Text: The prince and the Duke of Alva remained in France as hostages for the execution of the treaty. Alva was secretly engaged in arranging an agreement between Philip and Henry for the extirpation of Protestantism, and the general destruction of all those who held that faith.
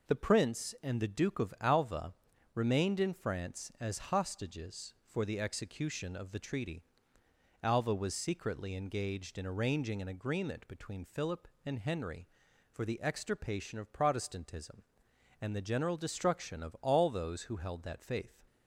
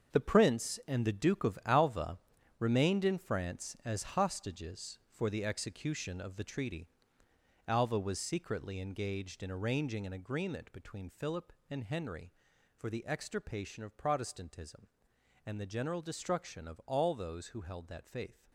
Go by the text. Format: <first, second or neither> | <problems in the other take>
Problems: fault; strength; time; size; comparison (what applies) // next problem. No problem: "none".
first | gets quieter; strong; throughout; 11 dB // pauses between "Alva" and "remained"; at 2.1 s; 0.42 s long; also in the first